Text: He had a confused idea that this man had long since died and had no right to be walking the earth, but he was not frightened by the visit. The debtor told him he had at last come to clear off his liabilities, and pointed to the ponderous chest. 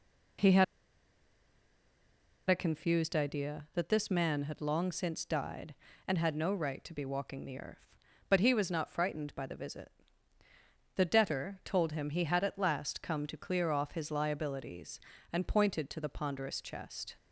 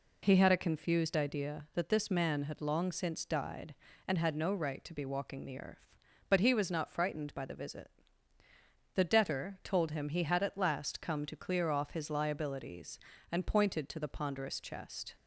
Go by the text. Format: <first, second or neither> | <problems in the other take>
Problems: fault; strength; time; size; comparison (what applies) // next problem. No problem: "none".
second | pauses between "had" and "a"; strong; at 0.6 s; 1.8 s long